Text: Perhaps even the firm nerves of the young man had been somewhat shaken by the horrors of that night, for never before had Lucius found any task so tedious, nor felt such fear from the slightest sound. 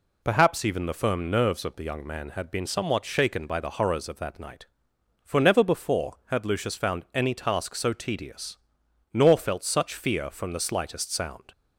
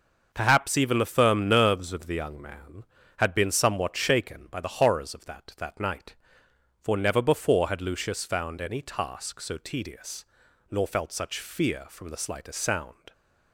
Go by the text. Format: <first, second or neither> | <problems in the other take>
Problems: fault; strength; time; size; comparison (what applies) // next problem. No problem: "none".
first | starts louder than the rest; until 1.3 s; 6 dB // says "that" twice; at 5.5 s